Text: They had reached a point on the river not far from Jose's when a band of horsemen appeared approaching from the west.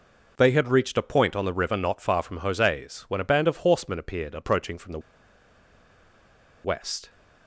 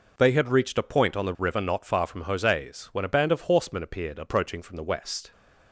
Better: second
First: pauses between "the" and "west"; strong; at 4.9 s; 1.6 s long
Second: none

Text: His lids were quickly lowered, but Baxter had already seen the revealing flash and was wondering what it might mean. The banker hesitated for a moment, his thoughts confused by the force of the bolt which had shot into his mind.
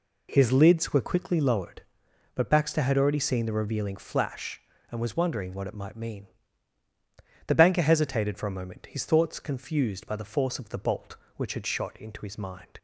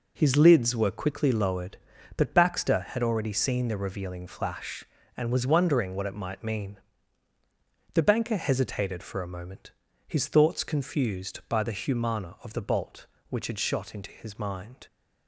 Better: first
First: none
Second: says "humana" for "force"; at 11.7 s

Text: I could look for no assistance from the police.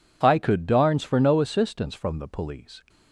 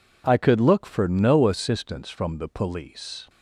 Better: second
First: says "darns" for "look"; at 0.6 s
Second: none

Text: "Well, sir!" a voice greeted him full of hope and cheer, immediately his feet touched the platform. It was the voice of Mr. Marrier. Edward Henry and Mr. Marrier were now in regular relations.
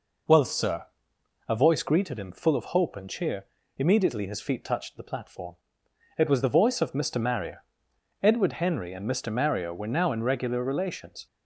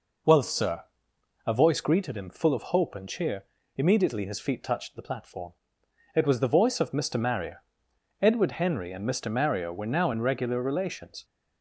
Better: neither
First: none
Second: none

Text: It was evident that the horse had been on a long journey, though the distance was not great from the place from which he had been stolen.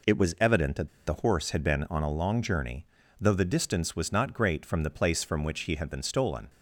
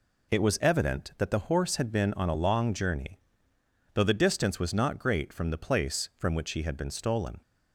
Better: second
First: pauses between "that" and "the"; slight; at 0.8 s; 0.17 s long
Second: none

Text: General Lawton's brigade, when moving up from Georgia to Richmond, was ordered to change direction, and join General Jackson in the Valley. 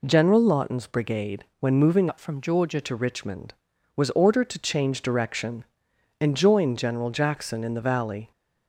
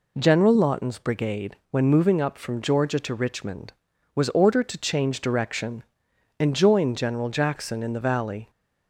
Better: second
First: changes voice from "up" to "Georgia"; from 2.0 to 2.8 s; 0.8 s long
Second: none

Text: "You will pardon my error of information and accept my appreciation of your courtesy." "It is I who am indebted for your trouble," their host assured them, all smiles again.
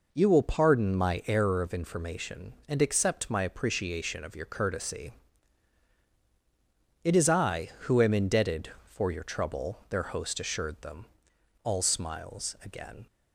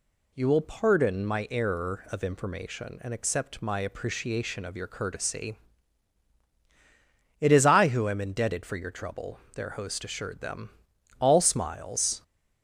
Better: first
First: none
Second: stops before "again"; at 12.2 s

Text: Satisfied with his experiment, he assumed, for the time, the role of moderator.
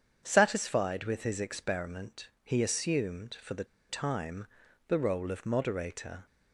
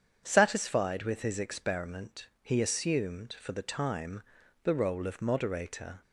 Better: second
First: starts louder than the rest; strong; until 1.2 s; 8 dB // pauses between "the" and "time"; slight; at 3.6 s; 0.24 s long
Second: starts louder than the rest; strong; until 1.2 s; 8 dB

